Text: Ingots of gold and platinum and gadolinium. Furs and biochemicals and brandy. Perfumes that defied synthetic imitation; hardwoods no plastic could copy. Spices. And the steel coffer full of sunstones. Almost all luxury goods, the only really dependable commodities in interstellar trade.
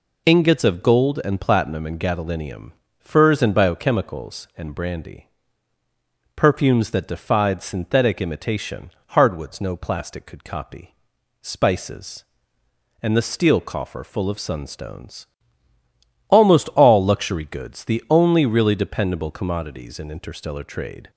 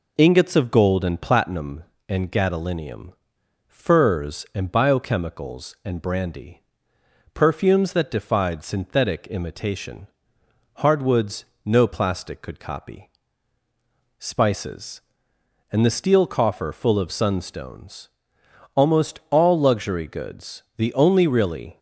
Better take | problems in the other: first | pauses between "hardwoods" and "no"; slight; at 11.4 s; 0.18 s long // stops before "dependable commodities in interstellar trade"; at 21.7 s

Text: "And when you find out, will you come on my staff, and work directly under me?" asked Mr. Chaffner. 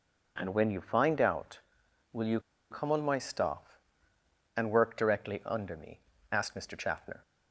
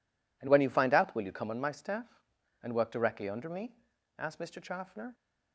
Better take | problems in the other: second | pauses between "you" and "come"; slight; at 2.3 s; 0.31 s long

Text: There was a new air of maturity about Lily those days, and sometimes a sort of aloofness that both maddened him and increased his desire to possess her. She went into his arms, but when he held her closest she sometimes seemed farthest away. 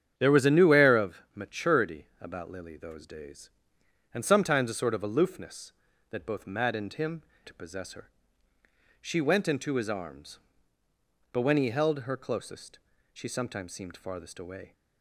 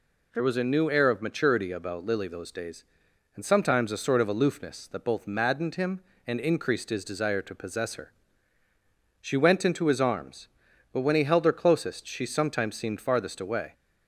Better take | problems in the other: second | starts louder than the rest; strong; until 1.1 s; 8.5 dB // pauses between "maturity" and "about"; slight; at 2.0 s; 0.16 s long // skips "and increased his desire"; at 7.3 s // pauses between "closest" and "she"; slight; at 12.7 s; 0.34 s long

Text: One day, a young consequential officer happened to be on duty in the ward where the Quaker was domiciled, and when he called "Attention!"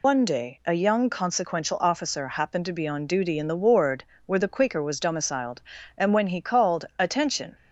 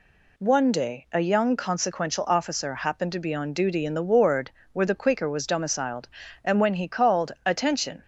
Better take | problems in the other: second | loses the start of "One"; at 0.0 s; 135 ms // pauses between "ward" and "where"; slight; at 4.0 s; 0.24 s long; slight in the second

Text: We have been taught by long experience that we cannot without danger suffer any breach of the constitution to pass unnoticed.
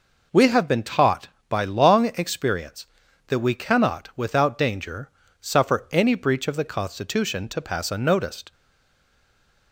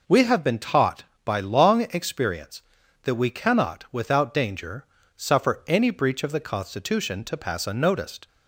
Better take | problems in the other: second | pauses between "danger" and "suffer"; slight; at 5.0 s; 0.32 s long; slight in the second // stays silent after the last word; noticeable; from 8.5 s on; 1.2 s long

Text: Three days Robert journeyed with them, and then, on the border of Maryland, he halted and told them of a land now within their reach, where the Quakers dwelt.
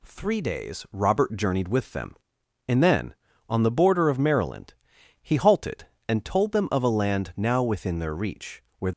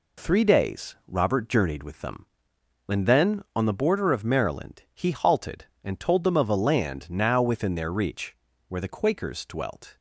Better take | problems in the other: second | stops before "the Quakers dwelt"; at 8.9 s

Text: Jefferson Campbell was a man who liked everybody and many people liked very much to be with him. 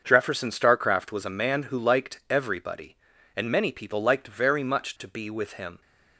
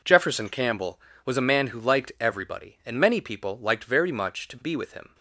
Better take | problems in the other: second | starts louder than the rest; until 1.0 s; 6.5 dB // says "Starcraft" for "Campbell"; at 0.4 s

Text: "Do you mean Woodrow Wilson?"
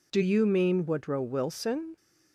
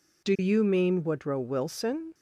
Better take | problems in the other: neither | none

